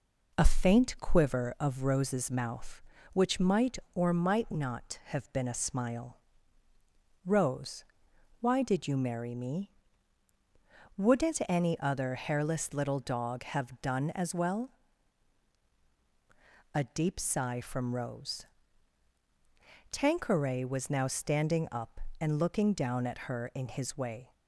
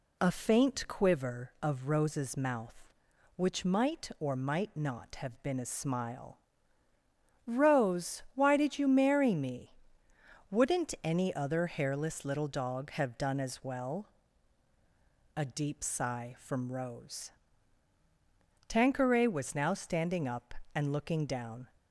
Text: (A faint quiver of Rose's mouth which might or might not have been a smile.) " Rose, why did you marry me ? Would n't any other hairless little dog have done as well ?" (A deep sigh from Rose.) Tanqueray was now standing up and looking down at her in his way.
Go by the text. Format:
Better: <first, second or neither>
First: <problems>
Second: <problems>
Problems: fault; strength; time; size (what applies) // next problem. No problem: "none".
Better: first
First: none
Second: stops before "at her in his way"; at 21.7 s